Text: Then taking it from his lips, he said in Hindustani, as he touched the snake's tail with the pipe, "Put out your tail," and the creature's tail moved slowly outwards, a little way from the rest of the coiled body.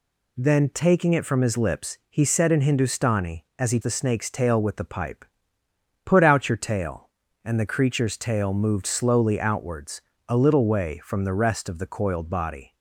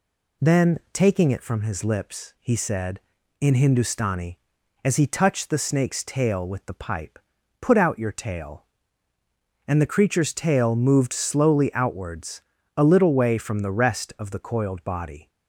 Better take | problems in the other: second | skips "touched"; at 3.8 s

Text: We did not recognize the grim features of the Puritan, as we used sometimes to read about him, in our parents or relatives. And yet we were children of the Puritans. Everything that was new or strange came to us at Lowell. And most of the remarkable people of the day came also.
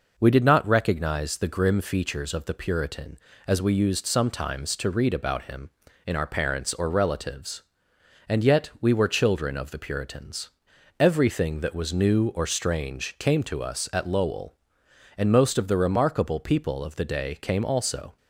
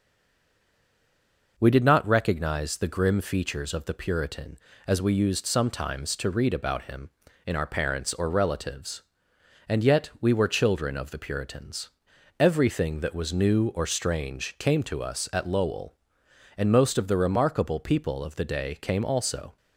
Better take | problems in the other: first | stays silent before the first word; noticeable; until 1.5 s; 1.5 s long

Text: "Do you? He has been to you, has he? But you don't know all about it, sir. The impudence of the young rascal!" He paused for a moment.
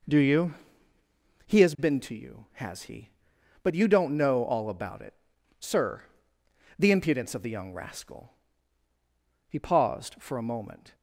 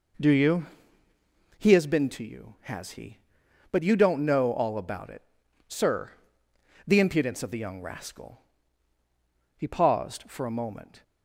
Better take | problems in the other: neither | none

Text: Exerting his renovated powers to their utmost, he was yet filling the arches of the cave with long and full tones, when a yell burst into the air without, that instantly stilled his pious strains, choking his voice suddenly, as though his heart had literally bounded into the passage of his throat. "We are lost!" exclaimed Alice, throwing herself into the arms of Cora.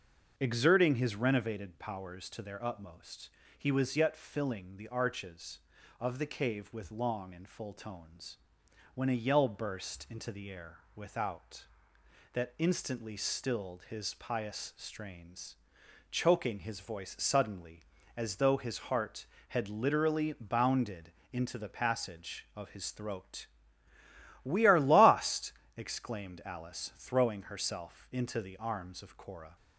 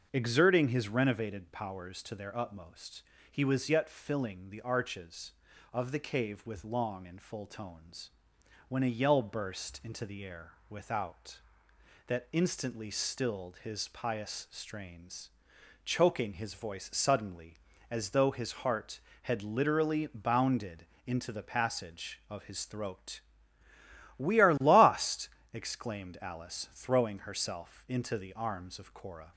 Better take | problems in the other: neither | starts louder than the rest; the same in both // pauses between "bounded" and "into"; slight; the same in both

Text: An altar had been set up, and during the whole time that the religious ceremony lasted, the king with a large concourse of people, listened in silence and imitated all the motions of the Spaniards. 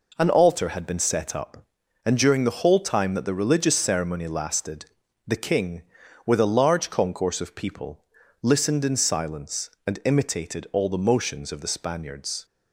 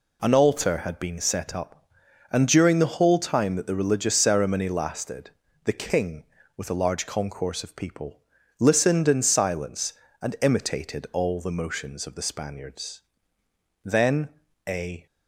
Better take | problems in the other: first | goes on to say "Then a"; noticeable; from 13.8 s on; 1.2 s long

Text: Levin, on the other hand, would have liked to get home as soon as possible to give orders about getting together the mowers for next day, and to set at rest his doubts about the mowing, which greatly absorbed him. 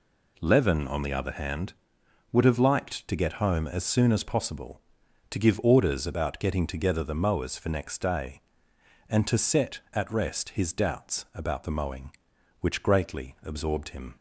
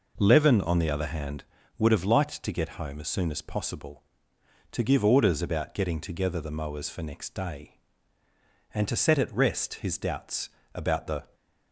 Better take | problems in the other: first | pauses between "doubts" and "about"; slight; at 10.4 s; 0.26 s long // stops before "mowing which greatly absorbed him"; at 11.3 s

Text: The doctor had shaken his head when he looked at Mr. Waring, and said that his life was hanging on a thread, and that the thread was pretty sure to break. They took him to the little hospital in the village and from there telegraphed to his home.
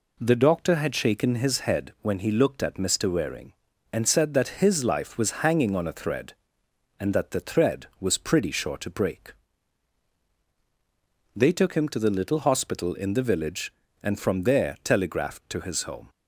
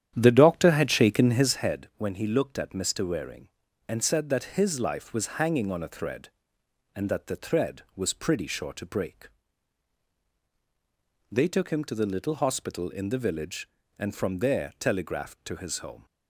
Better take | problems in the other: first | starts louder than the rest; strong; until 1.7 s; 10 dB

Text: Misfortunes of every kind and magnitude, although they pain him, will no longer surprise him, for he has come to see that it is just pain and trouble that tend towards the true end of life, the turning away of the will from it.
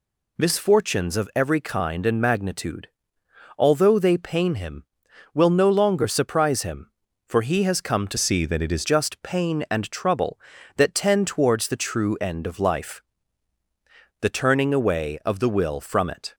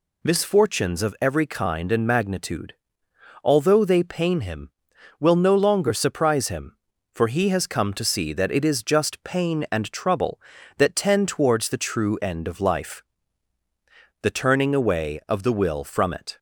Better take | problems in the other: second | changes voice from "see" to "is"; from 8.1 to 8.8 s; 0.7 s long

